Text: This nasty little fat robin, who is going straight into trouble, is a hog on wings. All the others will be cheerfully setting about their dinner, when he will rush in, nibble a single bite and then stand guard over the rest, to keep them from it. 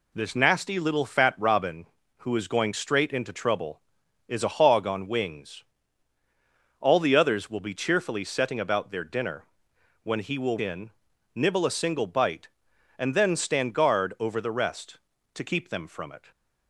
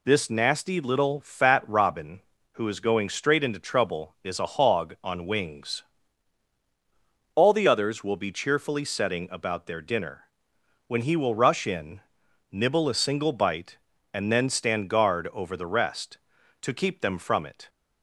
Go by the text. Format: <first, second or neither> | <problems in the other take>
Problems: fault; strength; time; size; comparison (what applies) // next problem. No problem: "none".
second | skips "rush"; at 10.5 s